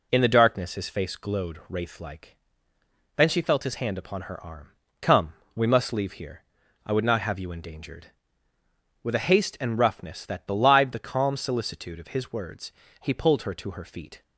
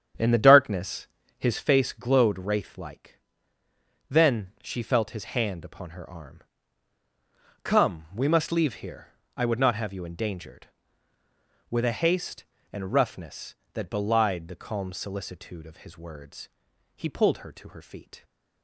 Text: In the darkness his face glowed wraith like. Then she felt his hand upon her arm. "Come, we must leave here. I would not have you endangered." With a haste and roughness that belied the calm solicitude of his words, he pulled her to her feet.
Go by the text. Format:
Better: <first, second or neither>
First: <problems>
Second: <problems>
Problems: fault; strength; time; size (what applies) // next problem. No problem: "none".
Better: first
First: none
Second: starts louder than the rest; strong; until 1.7 s; 8 dB // pauses between "darkness" and "his"; slight; at 1.0 s; 0.30 s long